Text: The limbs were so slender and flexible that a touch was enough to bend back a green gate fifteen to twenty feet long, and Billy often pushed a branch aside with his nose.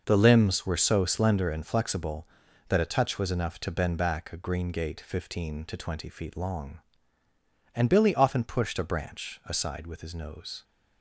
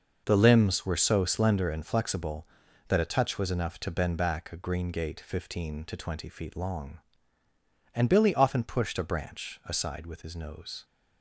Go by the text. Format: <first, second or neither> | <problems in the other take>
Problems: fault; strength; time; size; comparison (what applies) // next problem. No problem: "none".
neither | none